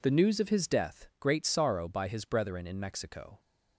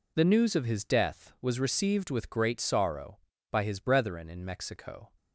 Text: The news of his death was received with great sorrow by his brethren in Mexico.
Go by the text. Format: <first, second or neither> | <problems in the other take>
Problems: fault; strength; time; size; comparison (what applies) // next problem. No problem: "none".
second | skips "was received with"; at 1.1 s